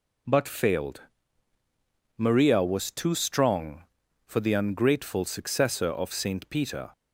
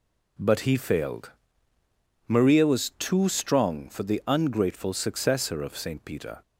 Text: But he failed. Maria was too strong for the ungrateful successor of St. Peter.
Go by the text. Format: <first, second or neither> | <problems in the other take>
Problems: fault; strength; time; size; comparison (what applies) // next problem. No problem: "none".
second | skips "he"; at 0.4 s